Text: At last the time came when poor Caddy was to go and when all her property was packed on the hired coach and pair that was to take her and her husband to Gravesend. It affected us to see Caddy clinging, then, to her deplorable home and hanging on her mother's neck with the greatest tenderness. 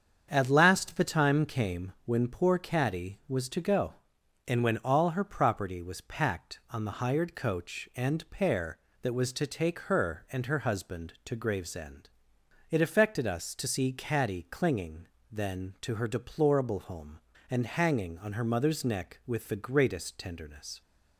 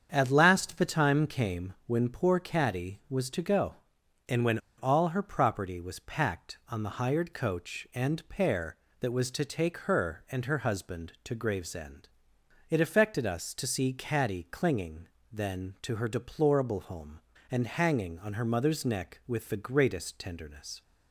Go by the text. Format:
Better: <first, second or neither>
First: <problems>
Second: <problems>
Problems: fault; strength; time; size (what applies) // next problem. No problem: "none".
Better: first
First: starts louder than the rest; strong; until 1.3 s; 7.5 dB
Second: starts louder than the rest; strong; until 1.1 s; 7.5 dB // pauses between "when" and "all"; slight; at 4.5 s; 0.19 s long